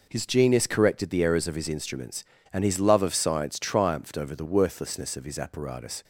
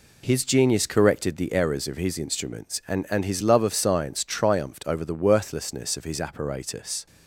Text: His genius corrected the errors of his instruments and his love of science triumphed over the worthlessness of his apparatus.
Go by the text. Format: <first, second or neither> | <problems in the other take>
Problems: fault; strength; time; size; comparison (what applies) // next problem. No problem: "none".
first | says "and" twice; at 3.1 s